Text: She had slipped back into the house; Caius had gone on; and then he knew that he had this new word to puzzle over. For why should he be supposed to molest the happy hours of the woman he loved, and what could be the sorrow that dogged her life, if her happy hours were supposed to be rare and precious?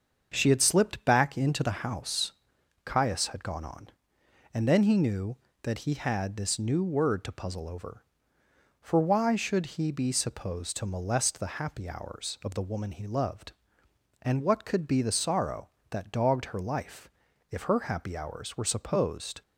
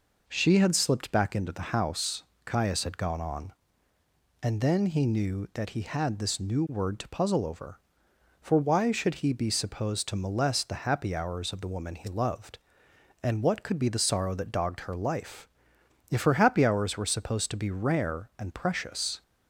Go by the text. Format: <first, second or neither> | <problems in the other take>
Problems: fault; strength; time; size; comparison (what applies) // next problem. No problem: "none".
second | starts louder than the rest; until 1.3 s; 6.5 dB // stops before "to be rare and precious"; at 19.4 s